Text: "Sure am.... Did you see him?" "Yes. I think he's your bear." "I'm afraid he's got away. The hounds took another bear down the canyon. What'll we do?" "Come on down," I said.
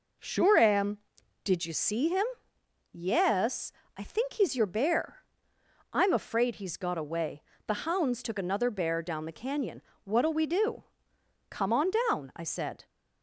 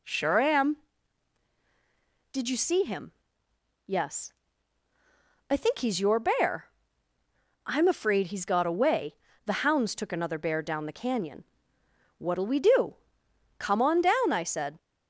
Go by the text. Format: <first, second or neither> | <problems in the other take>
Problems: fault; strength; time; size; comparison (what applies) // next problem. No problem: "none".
neither | none